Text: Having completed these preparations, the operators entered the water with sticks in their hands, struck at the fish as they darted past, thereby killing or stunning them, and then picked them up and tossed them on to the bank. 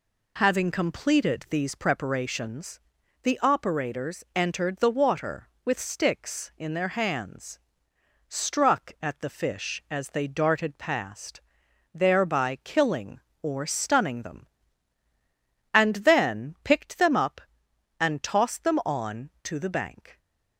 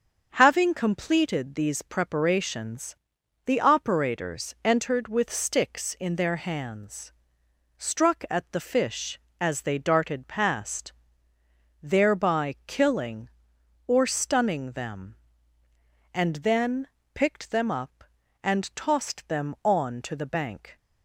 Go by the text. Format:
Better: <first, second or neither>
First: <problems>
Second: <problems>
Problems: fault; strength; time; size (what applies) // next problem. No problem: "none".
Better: first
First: none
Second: starts louder than the rest; until 1.3 s; 7 dB // skips "the water"; at 5.0 s // pauses between "then" and "picked"; slight; at 16.8 s; 0.26 s long